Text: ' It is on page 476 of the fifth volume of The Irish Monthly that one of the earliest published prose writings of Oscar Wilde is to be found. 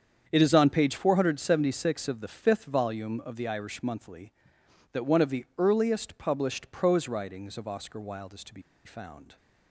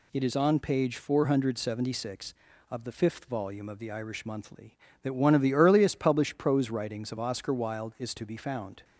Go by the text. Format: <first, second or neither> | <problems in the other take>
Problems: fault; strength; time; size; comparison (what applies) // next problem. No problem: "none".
second | starts louder than the rest; strong; until 1.2 s; 7.5 dB // pauses between "be" and "found"; slight; at 8.6 s; 0.24 s long